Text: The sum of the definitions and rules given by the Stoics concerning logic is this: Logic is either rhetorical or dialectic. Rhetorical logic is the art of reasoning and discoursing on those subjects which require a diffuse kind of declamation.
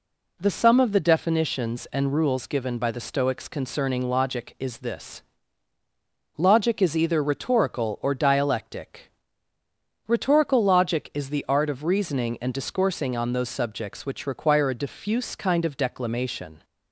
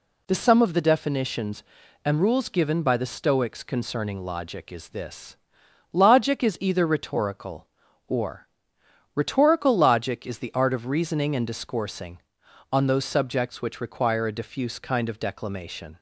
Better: first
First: none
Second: skips "dialectic"; at 8.7 s

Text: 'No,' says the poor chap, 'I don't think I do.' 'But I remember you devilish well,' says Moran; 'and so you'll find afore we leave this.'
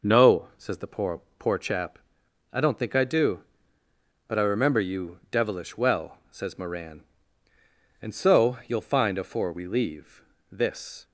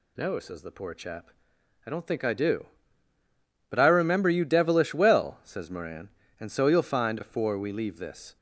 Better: second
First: says "poor" twice; at 1.3 s // pauses between "leave" and "this"; slight; at 10.2 s; 0.28 s long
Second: none

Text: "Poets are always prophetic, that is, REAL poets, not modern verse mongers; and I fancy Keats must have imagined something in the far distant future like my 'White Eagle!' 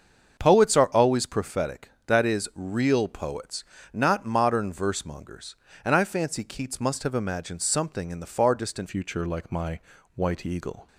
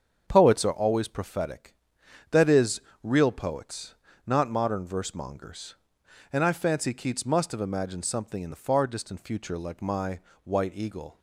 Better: second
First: starts louder than the rest; until 1.4 s; 6.5 dB // changes voice at "future"; from 8.8 s on; 2.0 s long // pauses between "my" and "White"; slight; at 9.7 s; 0.36 s long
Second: starts louder than the rest; strong; until 1.2 s; 7 dB // pauses between "my" and "White"; slight; at 10.2 s; 0.22 s long

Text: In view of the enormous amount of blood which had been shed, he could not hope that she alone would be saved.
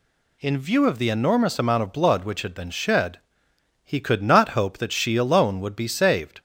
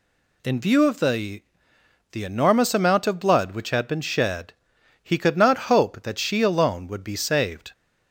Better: first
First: none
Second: says "the" twice; at 2.1 s

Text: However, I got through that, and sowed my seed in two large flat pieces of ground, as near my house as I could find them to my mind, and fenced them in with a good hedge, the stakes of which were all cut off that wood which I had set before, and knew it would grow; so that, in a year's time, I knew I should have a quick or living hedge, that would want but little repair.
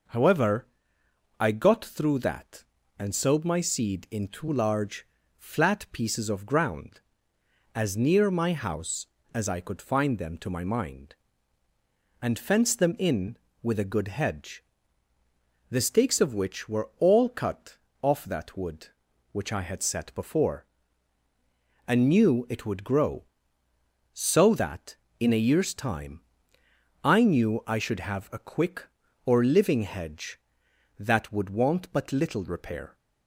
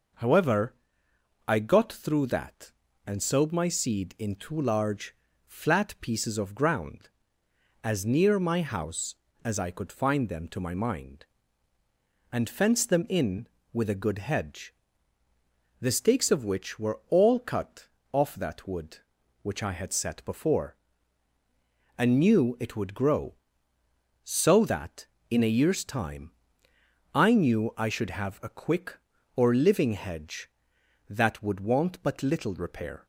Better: neither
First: pauses between "large" and "flat"; slight; at 5.0 s; 0.32 s long // pauses between "cut" and "off"; slight; at 17.7 s; 0.24 s long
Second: pauses between "large" and "flat"; slight; at 5.1 s; 0.32 s long // pauses between "cut" and "off"; slight; at 17.8 s; 0.24 s long

